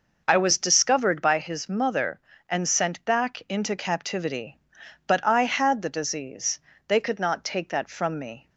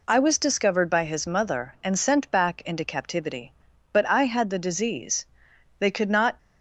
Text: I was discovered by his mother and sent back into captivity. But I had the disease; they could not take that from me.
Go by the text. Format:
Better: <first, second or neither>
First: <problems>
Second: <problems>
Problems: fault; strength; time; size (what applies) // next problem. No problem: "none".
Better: first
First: none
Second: stops before "take that from me"; at 6.3 s